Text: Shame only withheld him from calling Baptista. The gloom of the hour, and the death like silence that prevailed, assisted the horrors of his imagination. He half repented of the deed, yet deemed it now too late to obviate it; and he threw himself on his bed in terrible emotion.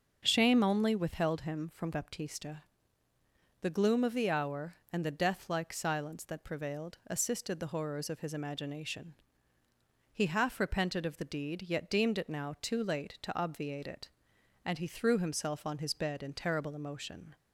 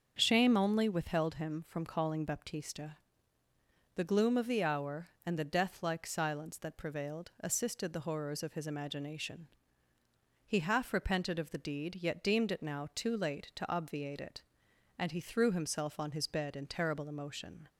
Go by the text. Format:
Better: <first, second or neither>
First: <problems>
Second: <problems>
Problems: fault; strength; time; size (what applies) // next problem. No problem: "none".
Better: second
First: starts louder than the rest; until 1.2 s; 6.5 dB // skips "calling"; at 1.9 s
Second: starts louder than the rest; until 1.1 s; 6.5 dB